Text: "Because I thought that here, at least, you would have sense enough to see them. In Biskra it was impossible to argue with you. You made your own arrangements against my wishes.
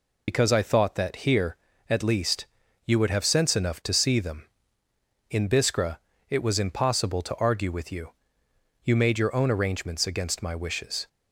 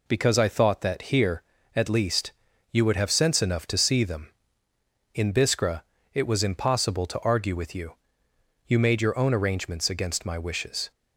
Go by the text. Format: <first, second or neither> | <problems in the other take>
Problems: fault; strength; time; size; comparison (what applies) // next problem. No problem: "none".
second | loses the start of "Because"; at 0.2 s; 60 ms // pauses between "Biskra" and "it"; slight; at 5.9 s; 0.30 s long; slight in the second